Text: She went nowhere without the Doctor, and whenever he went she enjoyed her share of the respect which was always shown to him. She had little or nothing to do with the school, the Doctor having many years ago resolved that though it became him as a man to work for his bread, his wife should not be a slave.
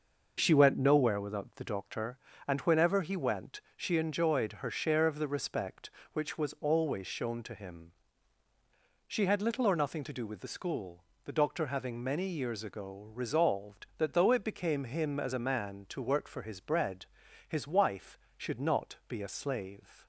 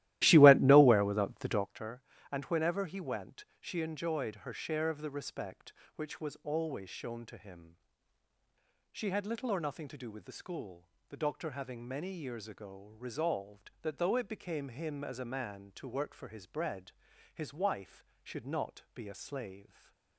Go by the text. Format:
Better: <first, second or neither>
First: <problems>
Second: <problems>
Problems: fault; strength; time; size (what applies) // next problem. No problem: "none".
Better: first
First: none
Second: starts louder than the rest; strong; until 1.7 s; 15 dB // stays silent after the last word; slight; from 19.6 s on; 0.5 s long